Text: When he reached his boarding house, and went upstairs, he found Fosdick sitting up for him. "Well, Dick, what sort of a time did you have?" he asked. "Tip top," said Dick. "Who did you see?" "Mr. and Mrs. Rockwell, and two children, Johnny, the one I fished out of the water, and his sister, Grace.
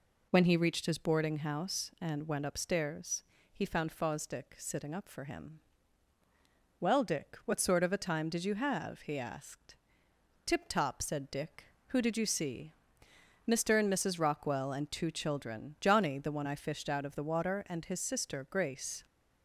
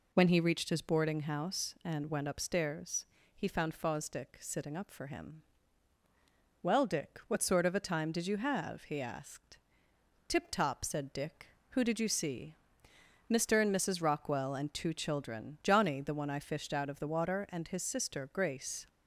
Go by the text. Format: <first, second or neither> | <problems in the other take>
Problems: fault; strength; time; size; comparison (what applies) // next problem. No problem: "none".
neither | none